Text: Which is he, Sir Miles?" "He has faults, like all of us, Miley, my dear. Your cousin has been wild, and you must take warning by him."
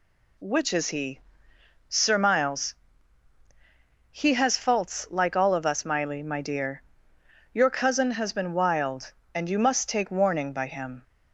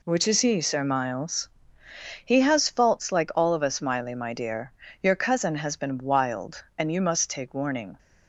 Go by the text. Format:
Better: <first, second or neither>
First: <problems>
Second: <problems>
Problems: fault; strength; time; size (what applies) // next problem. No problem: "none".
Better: first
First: none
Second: stops before "by him"; at 7.9 s